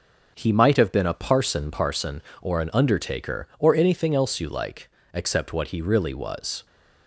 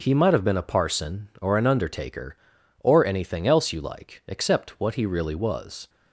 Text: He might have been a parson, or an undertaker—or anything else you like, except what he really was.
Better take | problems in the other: second | starts louder than the rest; noticeable; until 1.3 s; 6 dB; noticeable in the second // says "parson" twice; at 1.7 s

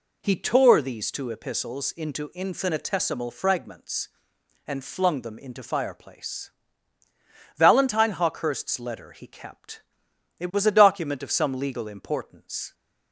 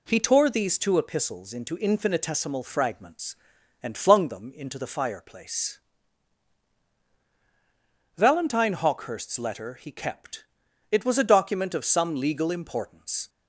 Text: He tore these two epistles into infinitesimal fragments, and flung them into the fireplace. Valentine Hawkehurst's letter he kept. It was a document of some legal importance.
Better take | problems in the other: second | skips "the"; at 5.6 s

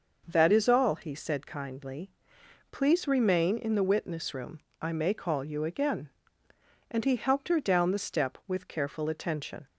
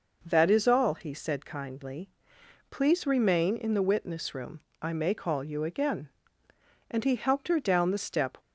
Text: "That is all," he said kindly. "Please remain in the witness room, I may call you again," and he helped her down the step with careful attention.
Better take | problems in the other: first | stops before "with careful attention"; at 8.3 s

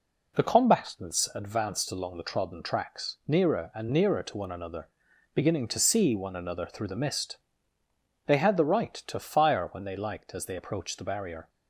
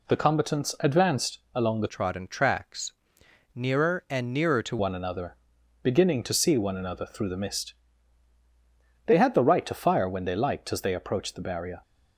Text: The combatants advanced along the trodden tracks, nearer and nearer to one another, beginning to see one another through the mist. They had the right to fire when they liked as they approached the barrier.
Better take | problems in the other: first | pauses between "advanced" and "along"; slight; at 1.3 s; 0.16 s long // changes voice from "trodden" to "to"; from 1.8 to 4.7 s; 2.9 s long

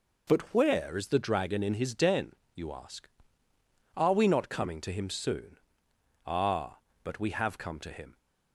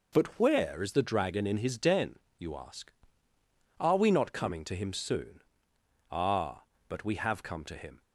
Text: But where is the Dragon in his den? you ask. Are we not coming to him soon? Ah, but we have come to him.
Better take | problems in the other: neither | none

